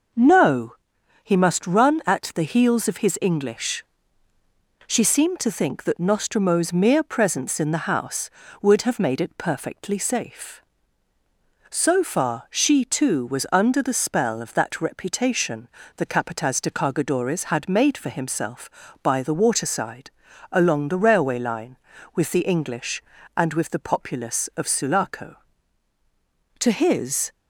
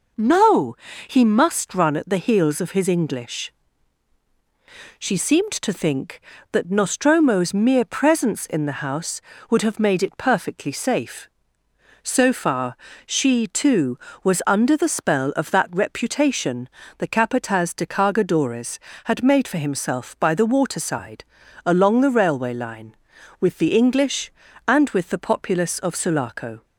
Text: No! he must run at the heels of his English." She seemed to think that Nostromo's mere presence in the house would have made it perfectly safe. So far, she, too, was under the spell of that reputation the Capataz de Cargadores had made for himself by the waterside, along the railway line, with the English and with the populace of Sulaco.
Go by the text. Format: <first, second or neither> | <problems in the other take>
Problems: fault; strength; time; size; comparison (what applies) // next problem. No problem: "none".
second | pauses between "reputation" and "the"; slight; at 15.6 s; 0.28 s long; slight in the second // goes on to say "To his"; noticeable; from 26.5 s on; 0.72 s long